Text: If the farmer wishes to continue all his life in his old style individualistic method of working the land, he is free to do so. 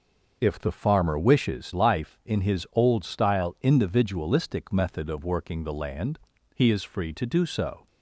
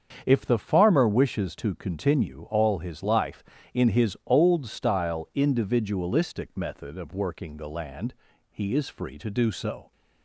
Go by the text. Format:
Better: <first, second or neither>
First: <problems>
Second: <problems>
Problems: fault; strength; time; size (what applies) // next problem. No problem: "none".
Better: second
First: starts louder than the rest; noticeable; until 1.4 s; 6 dB // skips "to continue all his"; at 1.7 s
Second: starts louder than the rest; strong; until 1.2 s; 7.5 dB